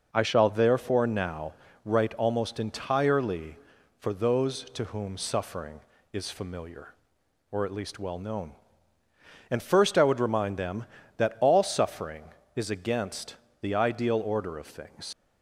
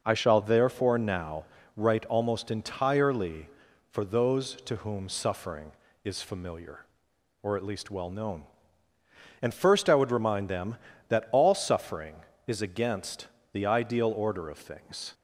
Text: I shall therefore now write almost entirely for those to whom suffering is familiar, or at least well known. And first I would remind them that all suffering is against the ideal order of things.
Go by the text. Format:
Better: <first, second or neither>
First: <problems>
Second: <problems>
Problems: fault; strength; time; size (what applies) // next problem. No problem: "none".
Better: second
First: pauses between "now" and "write"; slight; at 1.5 s; 0.32 s long // pauses between "against" and "the"; slight; at 13.3 s; 0.26 s long // leaves "things" unfinished; at 15.1 s; 90 ms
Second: pauses between "now" and "write"; slight; at 1.4 s; 0.32 s long // pauses between "against" and "the"; slight; at 13.2 s; 0.26 s long